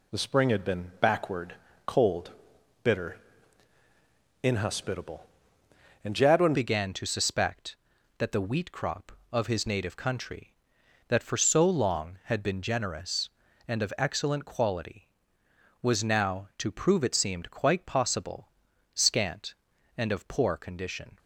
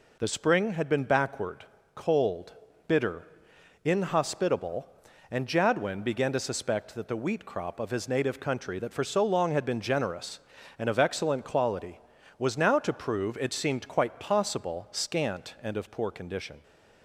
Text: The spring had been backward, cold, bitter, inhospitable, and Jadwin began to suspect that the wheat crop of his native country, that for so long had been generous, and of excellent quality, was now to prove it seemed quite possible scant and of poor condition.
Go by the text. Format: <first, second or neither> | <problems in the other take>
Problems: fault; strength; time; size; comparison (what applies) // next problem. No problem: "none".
second | changes voice at "began"; from 6.5 s on; 14.6 s long // pauses between "possible" and "scant"; at 18.4 s; 0.44 s long